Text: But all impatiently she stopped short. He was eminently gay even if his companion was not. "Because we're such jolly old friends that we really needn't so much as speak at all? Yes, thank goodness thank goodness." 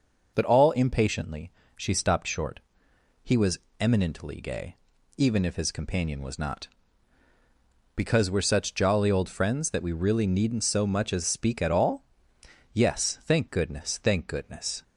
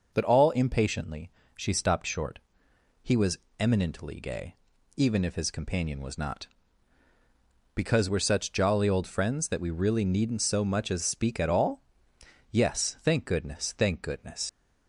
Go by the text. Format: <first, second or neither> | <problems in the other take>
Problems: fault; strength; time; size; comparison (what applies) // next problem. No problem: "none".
first | pauses between "impatiently" and "she"; slight; at 1.2 s; 0.26 s long; slight in the first // pauses between "was" and "eminently"; slight; at 3.3 s; 0.22 s long; slight in the first // pauses between "gay" and "even"; at 4.5 s; 0.40 s long; also in the first // leaves "goodness" unfinished; at 14.4 s; 80 ms